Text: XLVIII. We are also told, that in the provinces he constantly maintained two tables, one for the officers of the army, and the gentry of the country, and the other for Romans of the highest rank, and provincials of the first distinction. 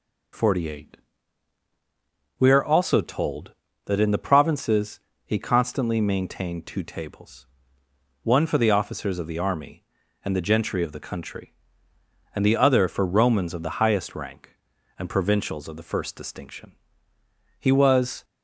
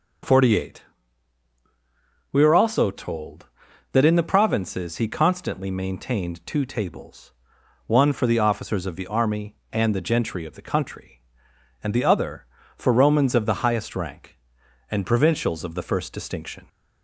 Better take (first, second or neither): second